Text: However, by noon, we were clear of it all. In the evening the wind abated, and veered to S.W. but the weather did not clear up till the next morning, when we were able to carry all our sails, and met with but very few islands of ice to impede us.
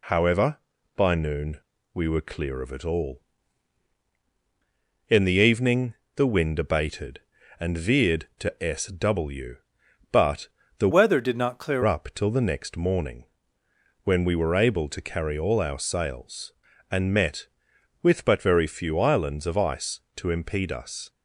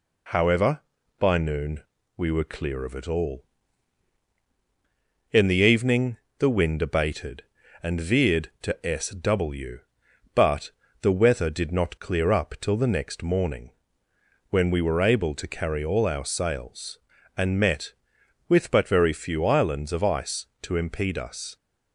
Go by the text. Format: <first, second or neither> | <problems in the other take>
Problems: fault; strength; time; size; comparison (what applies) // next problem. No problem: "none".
second | pauses between "evening" and "the"; slight; at 5.9 s; 0.22 s long; slight in the second // pauses between "but" and "the"; slight; at 10.4 s; 0.30 s long; slight in the second // changes voice from "weather" to "clear"; from 10.9 to 11.8 s; 0.9 s long